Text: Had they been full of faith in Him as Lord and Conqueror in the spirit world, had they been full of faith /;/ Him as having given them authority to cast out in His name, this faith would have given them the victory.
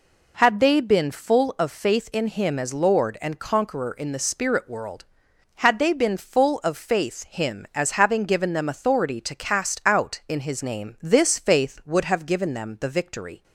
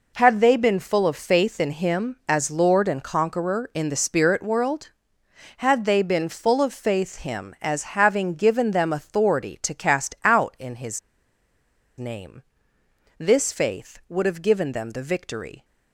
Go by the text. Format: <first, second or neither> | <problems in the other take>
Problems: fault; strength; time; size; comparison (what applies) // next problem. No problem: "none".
first | pauses between "His" and "name"; at 10.9 s; 0.98 s long